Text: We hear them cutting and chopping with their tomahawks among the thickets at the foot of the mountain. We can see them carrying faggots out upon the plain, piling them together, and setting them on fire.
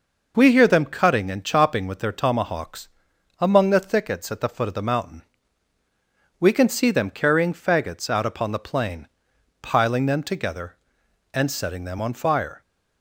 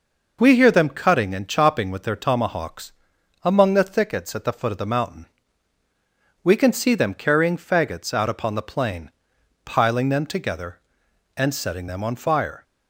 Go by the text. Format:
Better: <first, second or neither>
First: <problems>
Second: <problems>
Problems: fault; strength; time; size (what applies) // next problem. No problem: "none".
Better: neither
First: pauses between "tomahawks" and "among"; noticeable; at 2.8 s; 0.50 s long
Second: pauses between "tomahawks" and "among"; noticeable; at 2.9 s; 0.50 s long